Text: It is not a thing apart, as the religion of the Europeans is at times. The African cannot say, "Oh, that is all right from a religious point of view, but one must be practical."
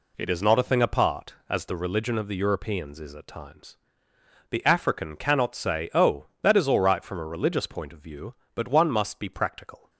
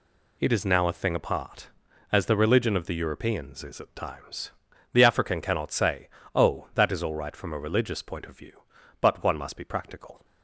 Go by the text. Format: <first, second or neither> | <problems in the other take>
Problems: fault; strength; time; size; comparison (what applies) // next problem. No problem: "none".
first | says "now" for "not"; at 0.6 s